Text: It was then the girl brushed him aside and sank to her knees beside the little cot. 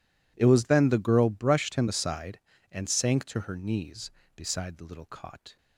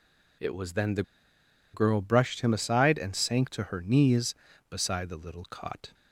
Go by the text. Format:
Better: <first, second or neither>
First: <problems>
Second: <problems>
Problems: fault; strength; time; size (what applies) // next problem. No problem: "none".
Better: first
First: none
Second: pauses between "the" and "girl"; noticeable; at 1.0 s; 0.71 s long